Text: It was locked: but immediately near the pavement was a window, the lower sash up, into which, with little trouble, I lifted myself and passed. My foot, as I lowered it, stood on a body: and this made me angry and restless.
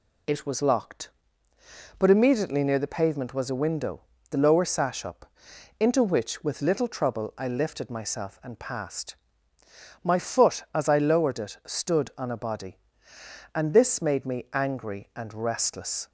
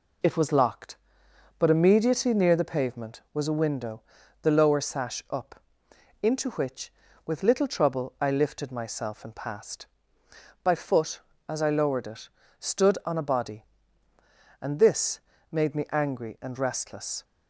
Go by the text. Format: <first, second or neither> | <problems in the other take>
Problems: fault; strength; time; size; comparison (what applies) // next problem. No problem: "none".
first | says "By" for "My"; at 10.6 s // pauses between "this" and "made"; slight; at 15.1 s; 0.30 s long